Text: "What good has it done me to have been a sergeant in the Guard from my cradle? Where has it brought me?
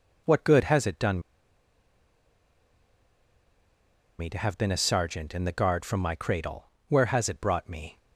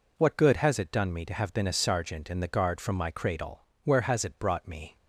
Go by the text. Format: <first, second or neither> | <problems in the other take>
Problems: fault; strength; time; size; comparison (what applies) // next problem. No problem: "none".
second | pauses between "done" and "me"; strong; at 1.1 s; 2.9 s long